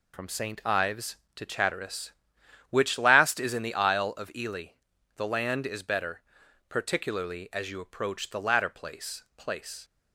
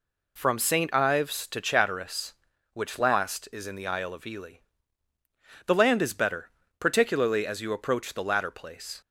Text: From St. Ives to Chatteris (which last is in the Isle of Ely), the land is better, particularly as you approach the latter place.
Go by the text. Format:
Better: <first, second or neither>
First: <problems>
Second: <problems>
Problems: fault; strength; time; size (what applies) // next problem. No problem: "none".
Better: second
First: says "place" twice; at 9.3 s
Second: none